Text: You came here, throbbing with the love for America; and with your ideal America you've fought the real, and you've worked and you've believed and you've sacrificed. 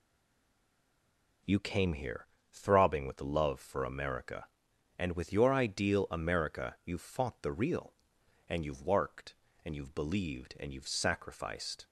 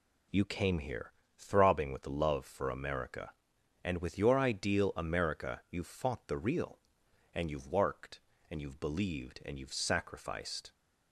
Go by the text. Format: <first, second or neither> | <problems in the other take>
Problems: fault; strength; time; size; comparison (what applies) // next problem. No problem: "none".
second | stays silent before the first word; noticeable; until 1.4 s; 1.4 s long